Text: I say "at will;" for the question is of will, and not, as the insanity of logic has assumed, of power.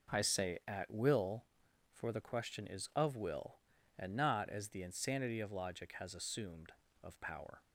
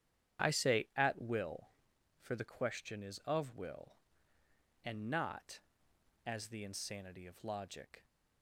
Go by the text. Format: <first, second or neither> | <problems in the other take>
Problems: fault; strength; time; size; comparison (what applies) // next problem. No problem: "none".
first | starts louder than the rest; strong; until 1.5 s; 9.5 dB // stops before "has assumed of power"; at 8.0 s